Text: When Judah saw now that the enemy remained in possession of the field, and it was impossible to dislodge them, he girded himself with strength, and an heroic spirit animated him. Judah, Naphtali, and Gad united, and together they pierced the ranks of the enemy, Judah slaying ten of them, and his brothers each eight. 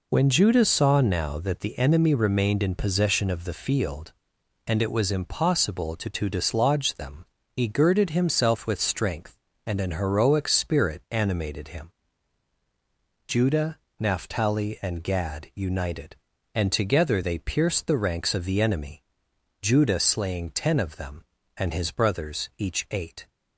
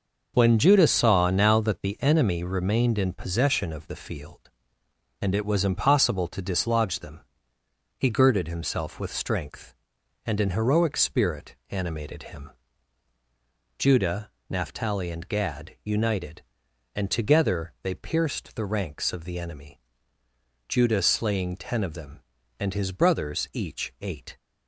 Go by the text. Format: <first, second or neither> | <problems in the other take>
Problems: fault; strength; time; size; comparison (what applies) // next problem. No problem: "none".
second | says "to" twice; at 6.0 s